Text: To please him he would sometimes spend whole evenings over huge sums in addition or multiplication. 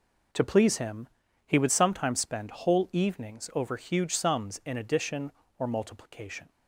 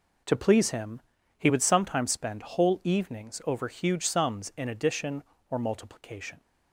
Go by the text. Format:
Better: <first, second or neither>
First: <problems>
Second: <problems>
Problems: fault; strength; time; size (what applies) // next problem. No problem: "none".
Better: neither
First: pauses between "him" and "he"; at 1.0 s; 0.38 s long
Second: pauses between "him" and "he"; at 1.0 s; 0.36 s long